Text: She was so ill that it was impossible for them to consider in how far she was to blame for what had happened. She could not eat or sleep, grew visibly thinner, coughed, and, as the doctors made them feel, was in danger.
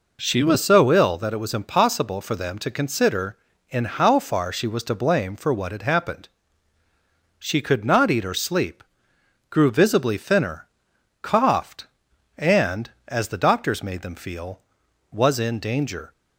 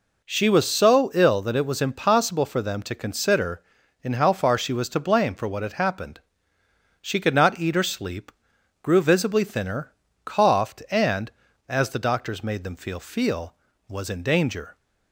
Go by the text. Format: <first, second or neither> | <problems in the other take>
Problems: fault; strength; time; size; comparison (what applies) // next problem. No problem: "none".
first | says "feel" twice; at 13.0 s